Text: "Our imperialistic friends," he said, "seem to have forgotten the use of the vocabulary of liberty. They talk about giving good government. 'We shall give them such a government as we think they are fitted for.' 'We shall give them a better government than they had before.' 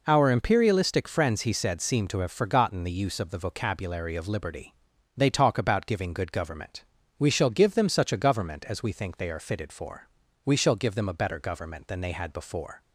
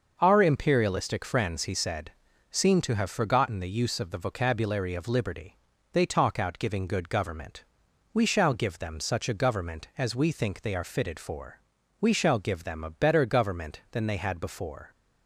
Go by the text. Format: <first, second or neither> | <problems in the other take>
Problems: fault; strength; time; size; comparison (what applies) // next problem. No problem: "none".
first | starts louder than the rest; noticeable; until 1.2 s; 6 dB // says "out" for "about"; at 6.3 s